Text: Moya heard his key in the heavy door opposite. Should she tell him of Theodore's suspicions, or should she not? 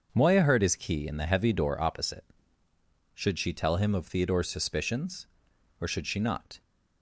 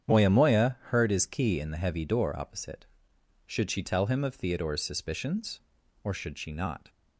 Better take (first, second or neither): first